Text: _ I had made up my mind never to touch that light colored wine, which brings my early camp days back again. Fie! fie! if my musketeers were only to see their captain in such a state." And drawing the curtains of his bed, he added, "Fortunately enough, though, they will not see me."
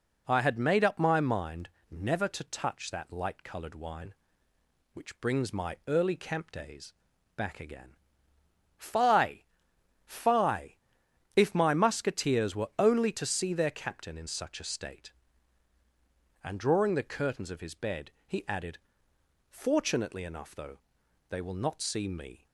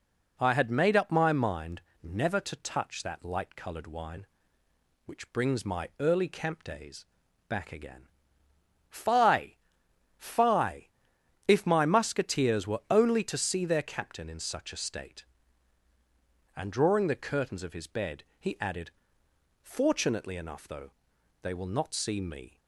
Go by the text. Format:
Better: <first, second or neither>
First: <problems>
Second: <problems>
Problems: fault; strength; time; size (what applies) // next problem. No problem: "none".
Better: neither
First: pauses between "mind" and "never"; slight; at 1.6 s; 0.22 s long // pauses between "days" and "back"; at 6.9 s; 0.42 s long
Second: pauses between "mind" and "never"; slight; at 1.8 s; 0.22 s long // pauses between "days" and "back"; at 7.0 s; 0.42 s long